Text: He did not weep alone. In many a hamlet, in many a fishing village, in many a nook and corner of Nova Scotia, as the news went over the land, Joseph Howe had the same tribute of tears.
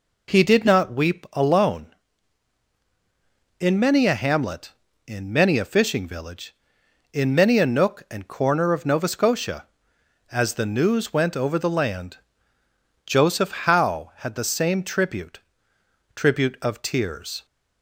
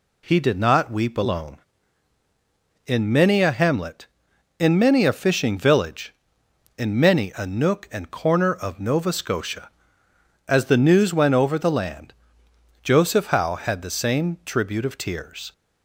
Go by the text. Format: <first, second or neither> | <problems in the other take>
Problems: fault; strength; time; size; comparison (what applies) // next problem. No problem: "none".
second | says "tribute" twice; at 16.1 s